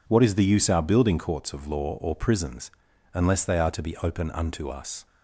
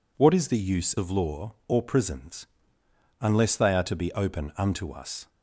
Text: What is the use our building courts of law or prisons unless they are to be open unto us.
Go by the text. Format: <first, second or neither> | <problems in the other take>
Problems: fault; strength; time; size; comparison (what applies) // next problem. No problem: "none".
first | skips "our building courts"; at 0.9 s // pauses between "prisons" and "unless"; noticeable; at 2.4 s; 0.74 s long; also in the first